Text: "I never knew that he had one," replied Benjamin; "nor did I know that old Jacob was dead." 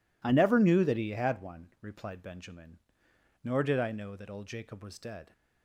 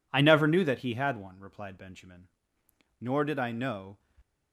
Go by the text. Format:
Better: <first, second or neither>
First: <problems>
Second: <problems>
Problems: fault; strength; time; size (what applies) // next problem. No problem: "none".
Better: first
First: none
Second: stops before "that old Jacob was dead"; at 4.1 s